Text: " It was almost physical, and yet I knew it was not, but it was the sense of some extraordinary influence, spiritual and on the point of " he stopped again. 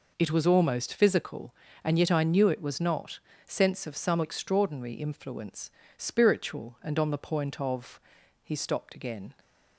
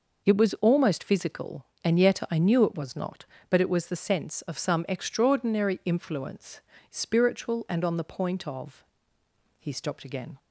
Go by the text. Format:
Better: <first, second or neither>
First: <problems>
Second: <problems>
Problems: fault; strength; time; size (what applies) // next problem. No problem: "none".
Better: second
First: skips "but it was the"; at 3.3 s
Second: none